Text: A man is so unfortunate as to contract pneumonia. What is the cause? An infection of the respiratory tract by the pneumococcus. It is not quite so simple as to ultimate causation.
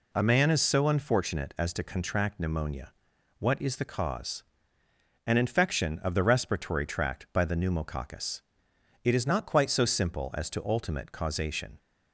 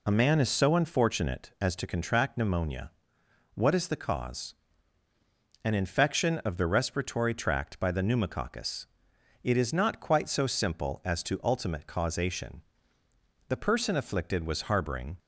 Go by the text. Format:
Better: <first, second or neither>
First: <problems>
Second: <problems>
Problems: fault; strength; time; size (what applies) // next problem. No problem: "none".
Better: first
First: none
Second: goes on to say "The person afflicted was harboring"; strong; from 13.4 s on; 1.7 s long